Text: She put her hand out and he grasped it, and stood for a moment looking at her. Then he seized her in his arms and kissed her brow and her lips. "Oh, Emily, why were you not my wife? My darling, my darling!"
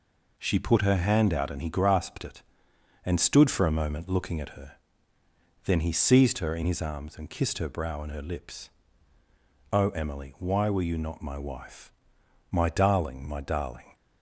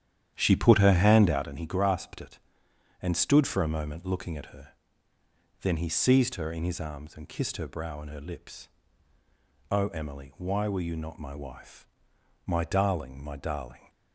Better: first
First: none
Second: starts louder than the rest; strong; until 1.5 s; 10 dB

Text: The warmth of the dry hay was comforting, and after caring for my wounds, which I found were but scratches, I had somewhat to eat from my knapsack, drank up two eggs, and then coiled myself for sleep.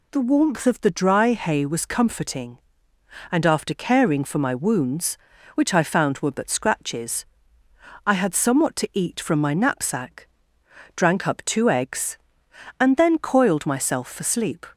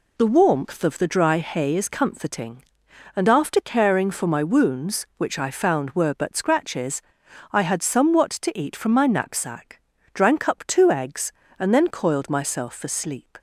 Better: first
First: none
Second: says "is" for "was"; at 1.7 s

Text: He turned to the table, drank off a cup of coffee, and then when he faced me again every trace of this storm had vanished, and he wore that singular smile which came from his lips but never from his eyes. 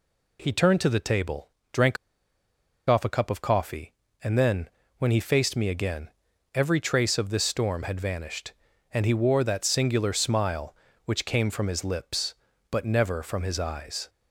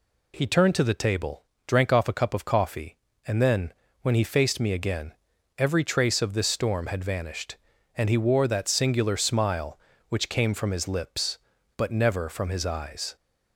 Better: second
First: pauses between "drank" and "off"; noticeable; at 1.9 s; 0.92 s long // pauses between "then" and "when"; slight; at 4.6 s; 0.28 s long // pauses between "again" and "every"; at 6.0 s; 0.44 s long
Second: pauses between "then" and "when"; slight; at 3.7 s; 0.28 s long // pauses between "again" and "every"; at 5.1 s; 0.44 s long

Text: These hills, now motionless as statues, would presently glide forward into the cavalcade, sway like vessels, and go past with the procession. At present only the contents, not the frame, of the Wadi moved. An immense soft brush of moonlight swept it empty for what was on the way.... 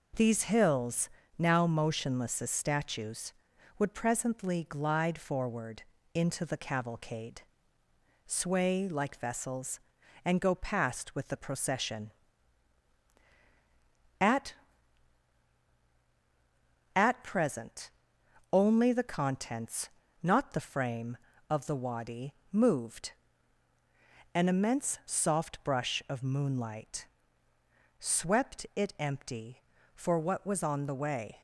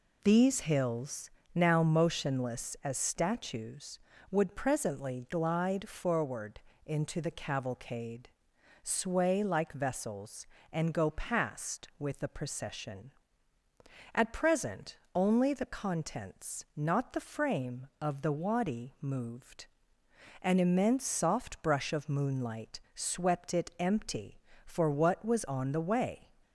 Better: second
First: pauses between "forward" and "into"; slight; at 5.8 s; 0.30 s long // says "At" twice; at 16.9 s // pauses between "present" and "only"; noticeable; at 17.9 s; 0.62 s long // pauses between "Wadi" and "moved"; slight; at 22.3 s; 0.20 s long // pauses between "moonlight" and "swept"; noticeable; at 27.0 s; 0.94 s long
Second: pauses between "forward" and "into"; slight; at 6.6 s; 0.24 s long // pauses between "present" and "only"; slight; at 14.9 s; 0.18 s long

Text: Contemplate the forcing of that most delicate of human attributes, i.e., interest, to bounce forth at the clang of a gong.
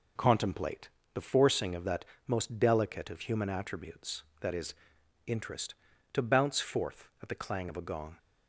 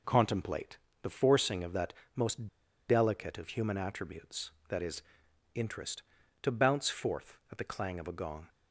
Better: first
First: pauses between "Contemplate" and "the"; slight; at 0.8 s; 0.24 s long // pauses between "that" and "most"; slight; at 2.0 s; 0.22 s long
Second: pauses between "Contemplate" and "the"; slight; at 0.7 s; 0.24 s long // pauses between "that" and "most"; slight; at 1.9 s; 0.22 s long // pauses between "most" and "delicate"; at 2.4 s; 0.41 s long

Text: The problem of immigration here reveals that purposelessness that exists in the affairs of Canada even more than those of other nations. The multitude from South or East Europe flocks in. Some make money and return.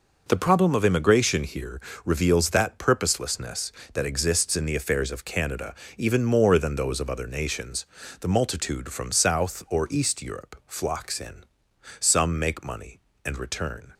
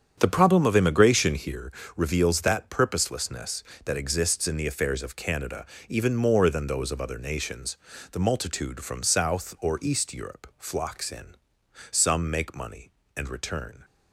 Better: first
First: pauses between "here" and "reveals"; slight; at 1.7 s; 0.24 s long // pauses between "Canada" and "even"; slight; at 5.7 s; 0.24 s long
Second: starts louder than the rest; strong; until 1.7 s; 7.5 dB // pauses between "here" and "reveals"; slight; at 1.7 s; 0.24 s long // pauses between "Canada" and "even"; slight; at 5.6 s; 0.24 s long

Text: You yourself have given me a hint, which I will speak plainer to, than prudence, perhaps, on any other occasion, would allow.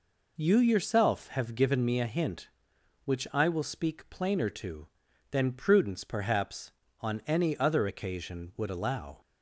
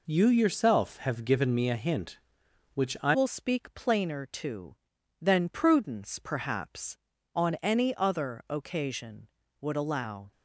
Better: first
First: none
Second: changes voice at "will"; from 3.1 s on; 7.2 s long

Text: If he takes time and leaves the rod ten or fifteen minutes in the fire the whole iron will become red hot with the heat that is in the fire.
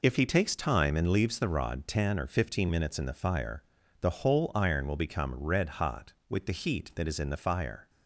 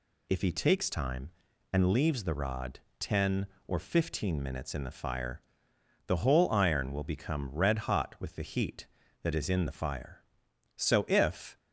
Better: first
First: pauses between "fire" and "the"; slight; at 3.6 s; 0.36 s long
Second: pauses between "rod" and "ten"; slight; at 2.7 s; 0.20 s long // pauses between "fire" and "the"; noticeable; at 5.4 s; 0.66 s long // goes on to say "So if"; noticeable; from 10.7 s on; 0.82 s long

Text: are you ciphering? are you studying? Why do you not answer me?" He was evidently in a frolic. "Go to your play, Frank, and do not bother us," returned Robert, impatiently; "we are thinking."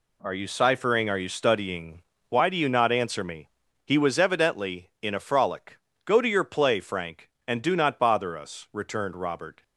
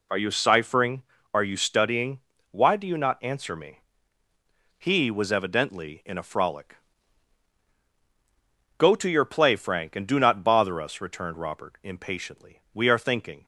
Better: second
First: stops before "impatiently we are thinking"; at 9.6 s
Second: none

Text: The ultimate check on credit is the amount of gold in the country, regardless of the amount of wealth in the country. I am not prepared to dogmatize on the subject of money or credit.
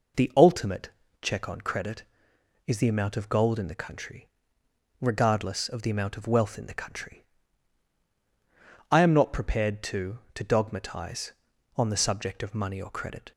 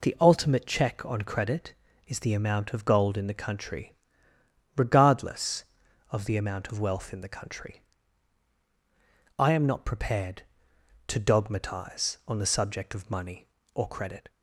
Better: second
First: pauses between "ultimate" and "check"; slight; at 0.8 s; 0.34 s long // says "to" twice; at 10.3 s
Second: none

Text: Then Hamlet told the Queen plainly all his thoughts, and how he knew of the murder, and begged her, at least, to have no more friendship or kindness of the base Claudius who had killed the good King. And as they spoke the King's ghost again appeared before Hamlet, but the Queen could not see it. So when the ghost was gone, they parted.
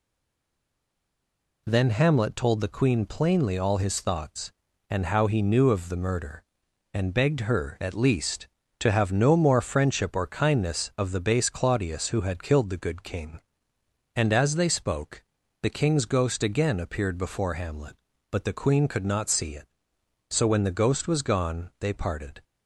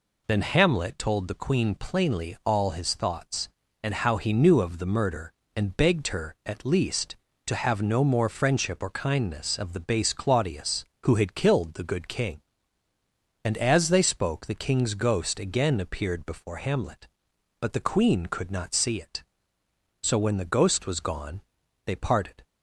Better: second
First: stays silent before the first word; noticeable; until 1.6 s; 1.6 s long // pauses between "spoke" and "the"; at 15.2 s; 0.38 s long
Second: none

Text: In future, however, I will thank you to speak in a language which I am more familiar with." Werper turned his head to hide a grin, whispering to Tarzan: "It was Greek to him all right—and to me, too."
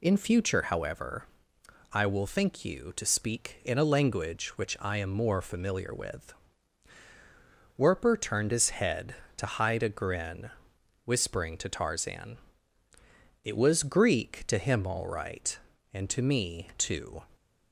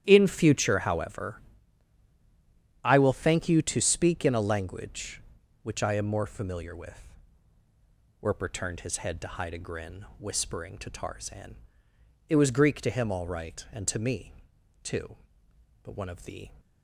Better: first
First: none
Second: starts louder than the rest; strong; until 1.0 s; 10.5 dB // goes on to say "But one of the"; noticeable; from 15.8 s on; 0.70 s long

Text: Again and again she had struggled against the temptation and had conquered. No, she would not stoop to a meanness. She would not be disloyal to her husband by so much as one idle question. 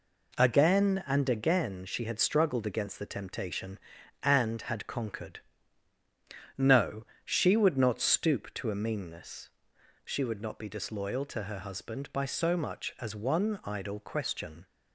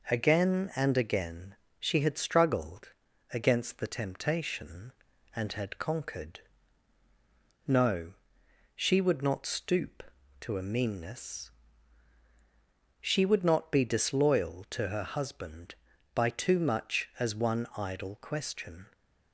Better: first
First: none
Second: pauses between "again" and "she"; slight; at 1.5 s; 0.24 s long // pauses between "struggled" and "against"; at 2.9 s; 0.40 s long // says "too" for "so"; at 16.2 s

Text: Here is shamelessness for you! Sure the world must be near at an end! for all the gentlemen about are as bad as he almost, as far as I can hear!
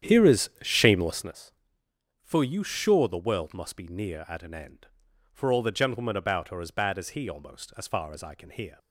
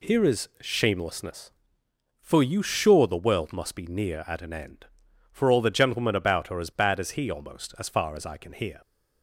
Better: second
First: starts louder than the rest; strong; until 1.3 s; 9.5 dB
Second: none

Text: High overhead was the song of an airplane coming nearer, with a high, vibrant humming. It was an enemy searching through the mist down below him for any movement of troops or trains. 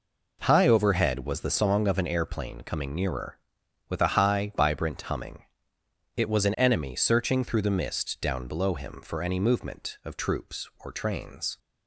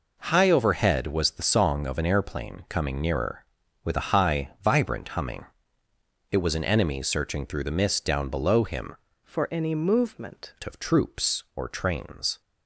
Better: first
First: none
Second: changes voice from "for" to "movement"; from 9.2 to 10.5 s; 1.3 s long

